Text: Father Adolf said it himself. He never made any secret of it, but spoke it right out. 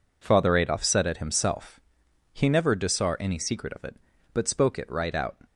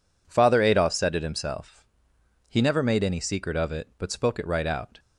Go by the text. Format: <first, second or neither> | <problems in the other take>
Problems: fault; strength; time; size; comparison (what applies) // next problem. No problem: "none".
second | says "disar" for "made"; at 2.7 s